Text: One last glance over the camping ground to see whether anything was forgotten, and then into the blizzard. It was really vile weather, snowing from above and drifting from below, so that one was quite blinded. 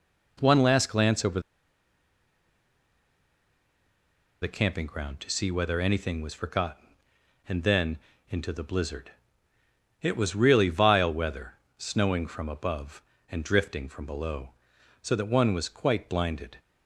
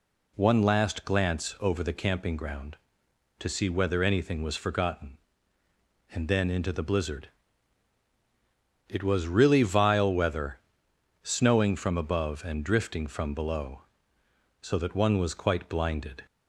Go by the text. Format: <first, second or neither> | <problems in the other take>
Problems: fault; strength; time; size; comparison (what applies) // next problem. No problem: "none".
second | pauses between "over" and "the"; strong; at 1.4 s; 3.0 s long // pauses between "then" and "into"; slight; at 7.9 s; 0.32 s long